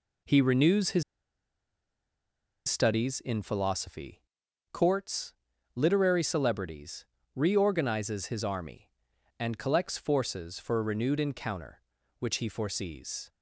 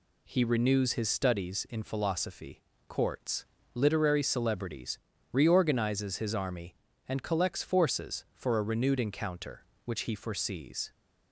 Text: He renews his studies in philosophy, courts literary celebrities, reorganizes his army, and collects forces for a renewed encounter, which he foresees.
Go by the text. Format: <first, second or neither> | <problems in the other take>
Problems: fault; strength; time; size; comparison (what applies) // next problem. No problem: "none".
second | pauses between "his" and "studies"; strong; at 1.0 s; 1.6 s long // pauses between "courts" and "literary"; at 5.3 s; 0.42 s long; slight in the second